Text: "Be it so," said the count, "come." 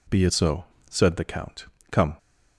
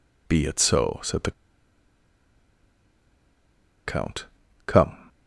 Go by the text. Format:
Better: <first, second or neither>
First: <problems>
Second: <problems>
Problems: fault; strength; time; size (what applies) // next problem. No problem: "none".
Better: first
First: none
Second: pauses between "the" and "count"; strong; at 1.3 s; 2.5 s long